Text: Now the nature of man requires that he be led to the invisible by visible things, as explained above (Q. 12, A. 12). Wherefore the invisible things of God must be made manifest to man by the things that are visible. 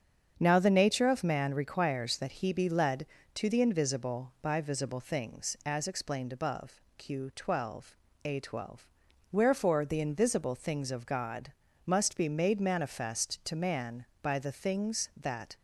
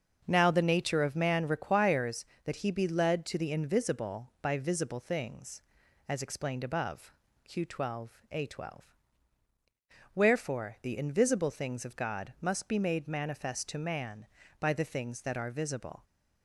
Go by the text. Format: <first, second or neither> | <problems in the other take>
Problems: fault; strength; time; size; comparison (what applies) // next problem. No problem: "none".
second | starts louder than the rest; strong; until 1.3 s; 7 dB; also in the second // pauses between "God" and "must"; slight; at 11.5 s; 0.32 s long // stops before "are visible"; at 15.5 s